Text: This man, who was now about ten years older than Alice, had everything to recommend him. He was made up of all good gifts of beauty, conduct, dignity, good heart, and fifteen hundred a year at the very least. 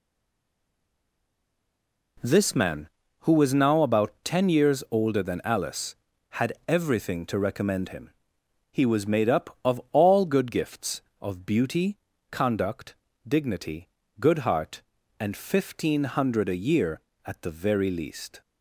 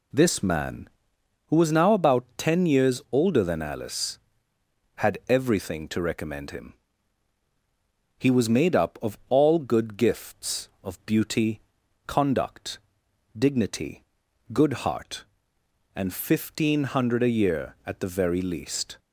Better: second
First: stays silent before the first word; until 2.1 s; 2.1 s long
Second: none

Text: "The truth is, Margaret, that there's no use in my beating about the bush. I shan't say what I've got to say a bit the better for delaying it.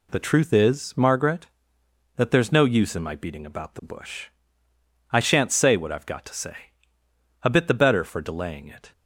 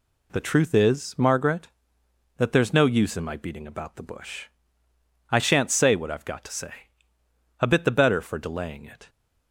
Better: neither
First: pauses between "say" and "a"; noticeable; at 6.5 s; 0.88 s long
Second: pauses between "say" and "a"; noticeable; at 6.7 s; 0.88 s long

